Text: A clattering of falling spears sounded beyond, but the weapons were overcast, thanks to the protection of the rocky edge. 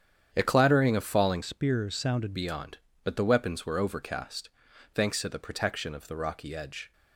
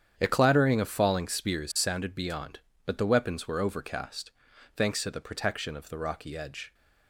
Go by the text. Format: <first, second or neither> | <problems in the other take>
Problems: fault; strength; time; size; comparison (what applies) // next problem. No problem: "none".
second | starts louder than the rest; strong; until 1.3 s; 9 dB; strong in the second // changes voice from "spears" to "sounded"; from 1.4 to 2.3 s; 0.9 s long